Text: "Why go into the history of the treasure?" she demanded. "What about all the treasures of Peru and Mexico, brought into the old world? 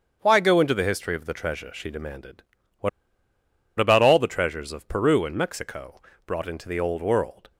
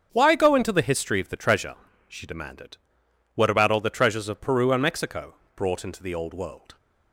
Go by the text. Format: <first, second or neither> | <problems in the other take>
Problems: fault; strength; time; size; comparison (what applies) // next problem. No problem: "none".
second | starts louder than the rest; strong; until 1.2 s; 7.5 dB; strong in the second // pauses between "What" and "about"; noticeable; at 2.8 s; 0.89 s long